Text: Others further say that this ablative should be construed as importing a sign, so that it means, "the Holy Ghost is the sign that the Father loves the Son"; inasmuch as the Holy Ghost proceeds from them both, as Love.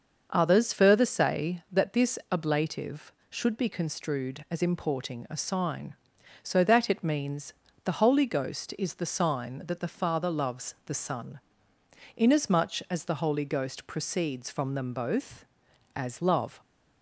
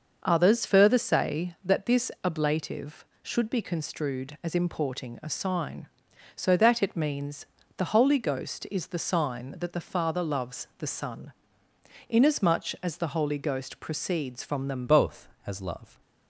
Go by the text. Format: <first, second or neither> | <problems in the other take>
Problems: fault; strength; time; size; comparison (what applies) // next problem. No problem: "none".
first | starts louder than the rest; until 1.2 s; 6.5 dB; also in the first // changes voice at "both"; from 14.8 s on; 1.2 s long